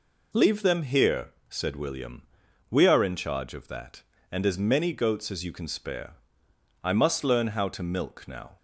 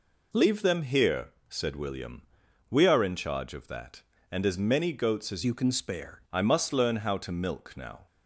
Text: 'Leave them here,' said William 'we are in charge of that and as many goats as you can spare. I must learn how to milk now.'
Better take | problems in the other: first | pauses between "William" and "we"; noticeable; at 2.2 s; 0.48 s long; noticeable in the first // changes voice from "you" to "spare"; from 5.4 to 6.2 s; 0.8 s long

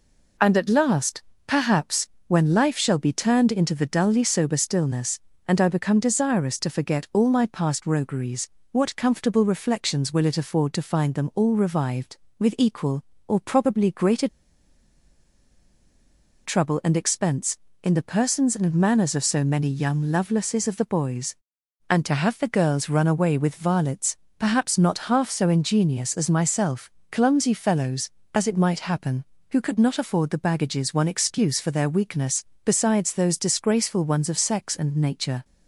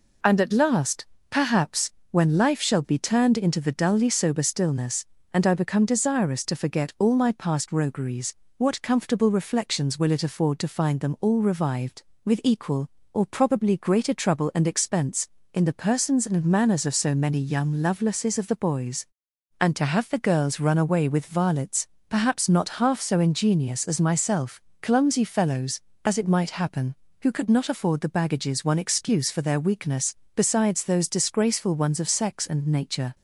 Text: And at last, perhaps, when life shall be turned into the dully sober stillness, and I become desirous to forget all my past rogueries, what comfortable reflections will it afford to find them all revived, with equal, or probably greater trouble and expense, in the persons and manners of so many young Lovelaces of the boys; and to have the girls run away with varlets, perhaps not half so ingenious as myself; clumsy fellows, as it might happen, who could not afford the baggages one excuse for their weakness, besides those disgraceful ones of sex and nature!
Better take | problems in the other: second | pauses between "greater" and "trouble"; strong; at 14.2 s; 2.1 s long

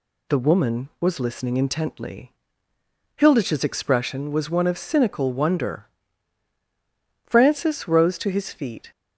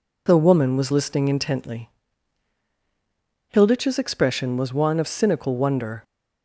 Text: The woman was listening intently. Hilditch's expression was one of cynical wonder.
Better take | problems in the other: second | goes on to say "Francis rose to his feet"; from 7.2 s on; 1.6 s long

